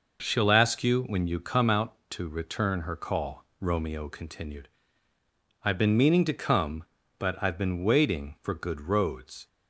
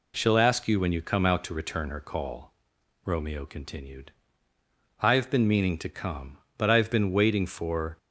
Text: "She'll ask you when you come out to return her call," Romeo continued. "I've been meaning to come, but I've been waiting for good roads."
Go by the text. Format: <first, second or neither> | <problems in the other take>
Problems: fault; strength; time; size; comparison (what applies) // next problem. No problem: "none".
first | stops before "good roads"; at 7.9 s